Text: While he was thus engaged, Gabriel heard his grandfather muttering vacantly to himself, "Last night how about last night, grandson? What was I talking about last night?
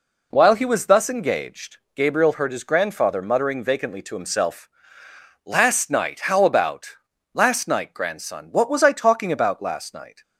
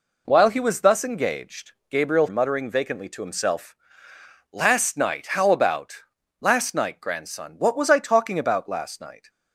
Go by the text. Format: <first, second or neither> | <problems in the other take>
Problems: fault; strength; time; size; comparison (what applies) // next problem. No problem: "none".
first | skips "heard his grandfather"; at 2.2 s // pauses between "about" and "last"; at 5.9 s; 0.44 s long; also in the first